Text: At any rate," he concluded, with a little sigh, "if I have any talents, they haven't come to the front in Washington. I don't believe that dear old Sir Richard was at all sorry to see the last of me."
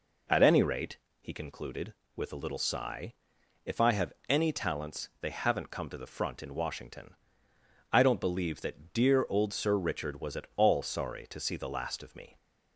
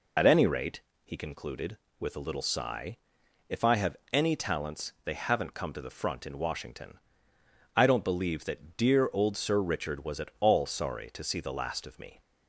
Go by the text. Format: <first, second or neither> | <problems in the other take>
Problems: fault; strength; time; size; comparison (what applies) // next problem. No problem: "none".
first | loses the start of "At"; at 0.1 s; 40 ms // pauses between "have" and "any"; slight; at 3.9 s; 0.16 s long; slight in the first